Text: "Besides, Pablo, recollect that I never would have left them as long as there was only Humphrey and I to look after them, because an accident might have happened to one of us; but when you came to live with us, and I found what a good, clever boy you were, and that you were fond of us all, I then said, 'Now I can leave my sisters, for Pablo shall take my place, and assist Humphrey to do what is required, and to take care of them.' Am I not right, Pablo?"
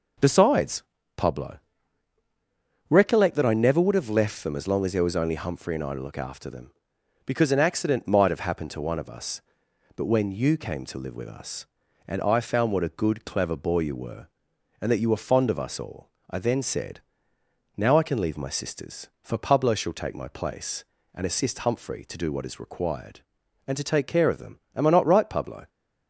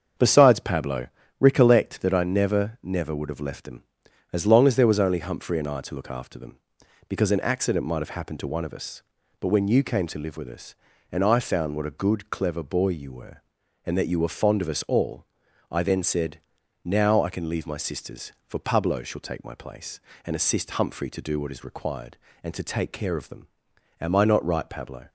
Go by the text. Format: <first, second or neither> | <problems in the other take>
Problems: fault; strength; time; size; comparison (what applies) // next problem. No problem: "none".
first | starts louder than the rest; strong; until 1.4 s; 7.5 dB // says "never" twice; at 2.8 s